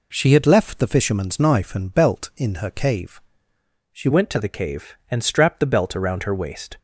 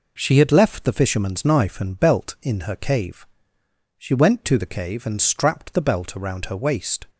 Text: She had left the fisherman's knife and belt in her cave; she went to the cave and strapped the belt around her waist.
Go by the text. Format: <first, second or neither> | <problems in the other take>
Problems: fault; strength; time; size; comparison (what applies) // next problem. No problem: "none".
second | changes voice at "went"; from 4.1 s on; 2.6 s long